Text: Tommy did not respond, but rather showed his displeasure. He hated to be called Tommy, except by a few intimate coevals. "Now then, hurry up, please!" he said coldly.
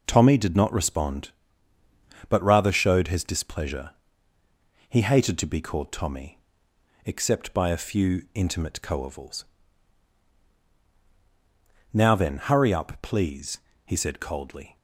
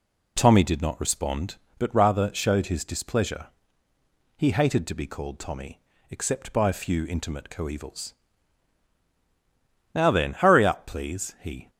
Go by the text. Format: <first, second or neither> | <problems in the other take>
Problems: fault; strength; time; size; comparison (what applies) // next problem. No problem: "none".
first | stops before "said coldly"; at 11.6 s